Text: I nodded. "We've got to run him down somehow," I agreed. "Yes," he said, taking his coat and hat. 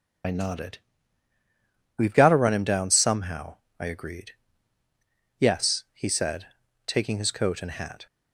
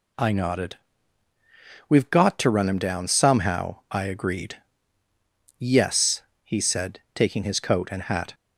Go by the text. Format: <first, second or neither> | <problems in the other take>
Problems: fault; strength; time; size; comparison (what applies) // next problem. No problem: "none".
second | loses the start of "I"; at 0.2 s; 45 ms